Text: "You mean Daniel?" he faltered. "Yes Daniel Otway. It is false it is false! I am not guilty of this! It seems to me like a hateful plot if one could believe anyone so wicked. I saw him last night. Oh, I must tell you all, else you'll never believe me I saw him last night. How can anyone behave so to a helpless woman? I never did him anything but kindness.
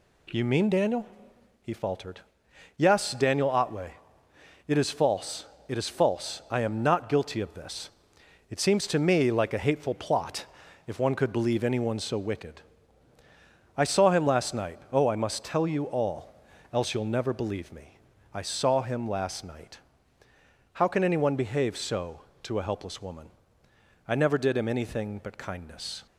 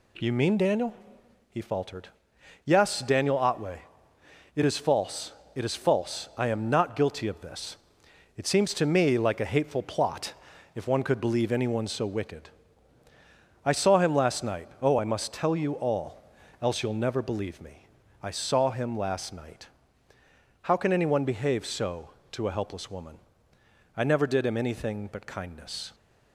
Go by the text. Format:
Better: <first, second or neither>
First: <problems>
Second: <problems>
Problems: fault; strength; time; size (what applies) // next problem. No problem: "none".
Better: neither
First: pauses between "false" and "it"; slight; at 5.4 s; 0.22 s long // pauses between "plot" and "if"; at 10.4 s; 0.40 s long // pauses between "me" and "I"; slight; at 17.9 s; 0.34 s long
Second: pauses between "false" and "it"; slight; at 5.3 s; 0.22 s long // pauses between "plot" and "if"; at 10.3 s; 0.40 s long // pauses between "me" and "I"; slight; at 17.8 s; 0.34 s long